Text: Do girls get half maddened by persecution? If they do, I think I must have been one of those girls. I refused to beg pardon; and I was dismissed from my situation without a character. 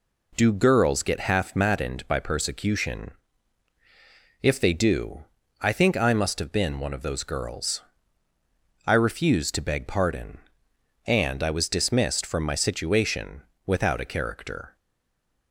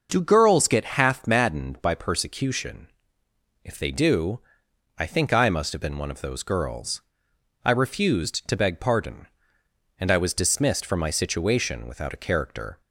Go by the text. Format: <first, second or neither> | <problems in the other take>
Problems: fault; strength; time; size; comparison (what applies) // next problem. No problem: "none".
second | pauses between "situation" and "without"; slight; at 13.4 s; 0.20 s long // stays silent after the last word; slight; from 14.7 s on; 0.8 s long